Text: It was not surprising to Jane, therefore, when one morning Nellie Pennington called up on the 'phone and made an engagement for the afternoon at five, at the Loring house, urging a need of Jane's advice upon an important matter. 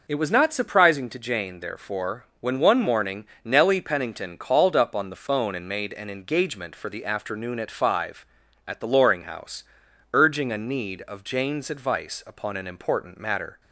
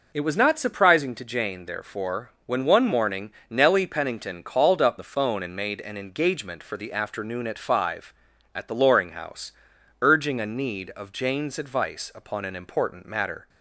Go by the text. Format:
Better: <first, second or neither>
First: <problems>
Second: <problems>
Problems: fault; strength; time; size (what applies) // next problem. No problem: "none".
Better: first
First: pauses between "morning" and "Nellie"; slight; at 3.2 s; 0.20 s long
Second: pauses between "morning" and "Nellie"; slight; at 3.3 s; 0.20 s long // skips "on"; at 4.9 s